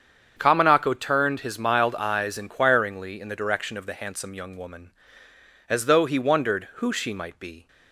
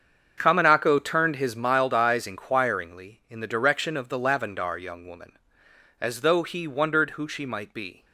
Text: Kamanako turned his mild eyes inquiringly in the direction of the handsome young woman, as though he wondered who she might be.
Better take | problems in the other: first | starts louder than the rest; strong; until 1.3 s; 7 dB; strong in the first // says "lavendar" for "handsome"; at 4.1 s

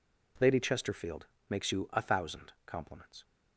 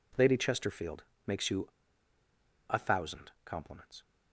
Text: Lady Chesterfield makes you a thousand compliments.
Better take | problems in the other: first | pauses between "Chesterfield" and "makes"; slight; at 1.0 s; 0.24 s long; slight in the first // pauses between "you" and "a"; at 1.6 s; 1.0 s long

